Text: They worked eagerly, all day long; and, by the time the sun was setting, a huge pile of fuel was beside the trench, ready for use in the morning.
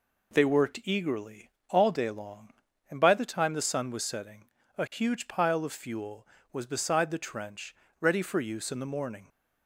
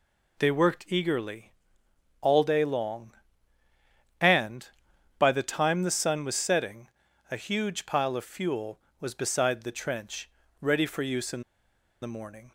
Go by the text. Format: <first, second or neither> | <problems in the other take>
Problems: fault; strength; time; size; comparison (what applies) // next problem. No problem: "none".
first | pauses between "in" and "the"; noticeable; at 11.4 s; 0.61 s long